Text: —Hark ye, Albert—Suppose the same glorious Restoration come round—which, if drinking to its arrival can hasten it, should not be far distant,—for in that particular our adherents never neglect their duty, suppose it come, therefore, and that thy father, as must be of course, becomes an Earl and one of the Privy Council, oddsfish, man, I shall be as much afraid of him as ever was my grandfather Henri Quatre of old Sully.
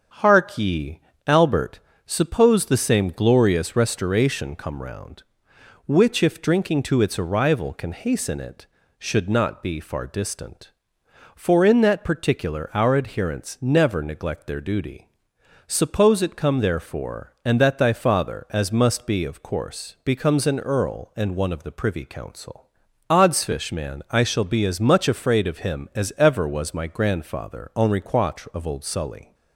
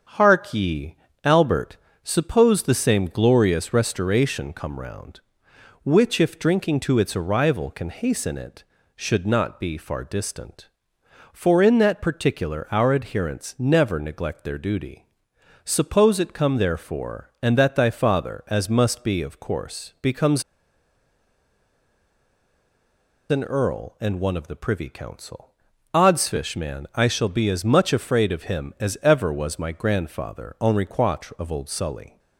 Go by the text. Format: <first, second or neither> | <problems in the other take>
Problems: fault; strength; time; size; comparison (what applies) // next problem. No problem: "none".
first | starts louder than the rest; strong; until 1.4 s; 7.5 dB; strong in the first // pauses between "becomes" and "an"; strong; at 20.4 s; 2.8 s long